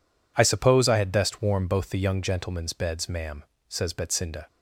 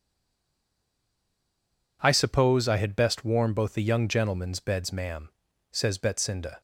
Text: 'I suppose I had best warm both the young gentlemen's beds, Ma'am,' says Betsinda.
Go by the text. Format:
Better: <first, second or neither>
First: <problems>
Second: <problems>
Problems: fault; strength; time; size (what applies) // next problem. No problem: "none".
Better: first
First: none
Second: stays silent before the first word; noticeable; until 2.0 s; 2.0 s long